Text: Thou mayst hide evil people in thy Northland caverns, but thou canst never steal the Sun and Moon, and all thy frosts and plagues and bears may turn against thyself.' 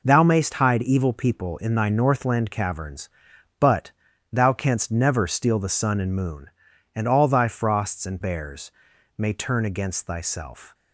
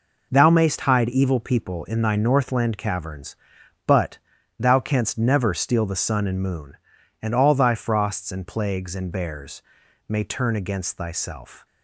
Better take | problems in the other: second | pauses between "but" and "thou"; at 3.9 s; 0.42 s long; also in the second // skips "plagues and"; at 8.2 s // pauses between "bears" and "may"; at 8.7 s; 0.44 s long; also in the second

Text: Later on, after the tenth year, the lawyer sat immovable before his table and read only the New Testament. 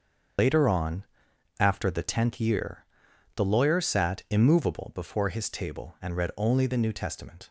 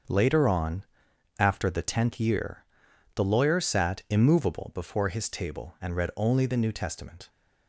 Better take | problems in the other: second | loses the start of "Later"; at 0.3 s; 130 ms // starts louder than the rest; until 1.9 s; 6.5 dB; also in the second

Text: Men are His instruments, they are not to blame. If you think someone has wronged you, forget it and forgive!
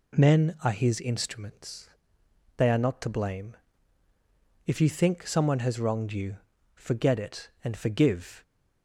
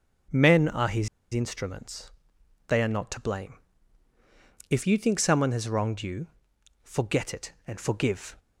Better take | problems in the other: first | starts louder than the rest; noticeable; until 1.5 s; 6 dB // pauses between "His" and "instruments"; slight; at 1.0 s; 0.24 s long

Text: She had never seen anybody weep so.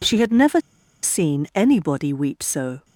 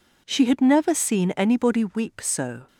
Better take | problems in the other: second | pauses between "never" and "seen"; at 0.5 s; 0.44 s long

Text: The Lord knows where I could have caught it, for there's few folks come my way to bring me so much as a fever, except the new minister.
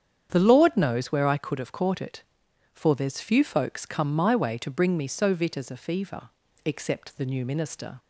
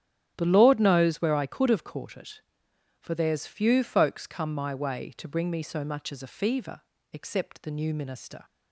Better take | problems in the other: second | starts louder than the rest; strong; until 1.3 s; 8.5 dB; strong in the second // says "vit" for "much"; at 5.3 s

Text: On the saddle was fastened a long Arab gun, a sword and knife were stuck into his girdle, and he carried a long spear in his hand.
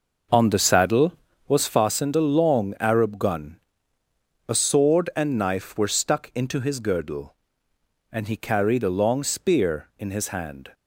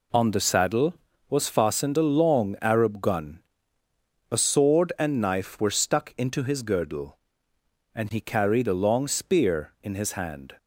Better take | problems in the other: second | starts louder than the rest; noticeable; until 1.8 s; 6 dB

